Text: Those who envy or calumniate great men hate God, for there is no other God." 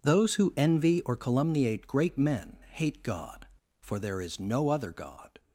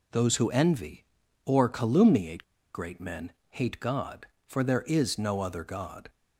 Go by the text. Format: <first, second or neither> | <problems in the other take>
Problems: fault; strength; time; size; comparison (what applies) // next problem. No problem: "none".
first | pauses between "calumniate" and "great"; slight; at 2.4 s; 0.31 s long // pauses between "men" and "hate"; slight; at 3.3 s; 0.16 s long